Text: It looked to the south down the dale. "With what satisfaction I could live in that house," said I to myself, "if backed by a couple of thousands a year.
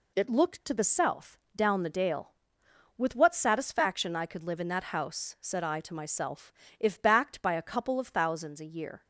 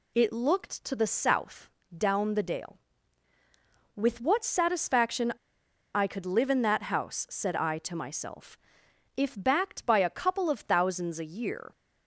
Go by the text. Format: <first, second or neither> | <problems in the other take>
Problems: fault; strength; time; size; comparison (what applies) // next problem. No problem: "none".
first | pauses between "south" and "down"; slight; at 1.6 s; 0.26 s long; slight in the first // pauses between "satisfaction" and "I"; noticeable; at 5.3 s; 0.63 s long